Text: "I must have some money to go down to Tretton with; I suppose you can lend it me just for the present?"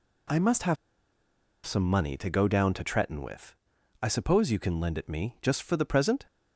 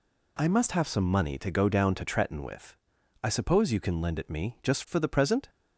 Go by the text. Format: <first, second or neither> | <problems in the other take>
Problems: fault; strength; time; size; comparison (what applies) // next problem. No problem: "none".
second | pauses between "have" and "some"; noticeable; at 0.7 s; 0.90 s long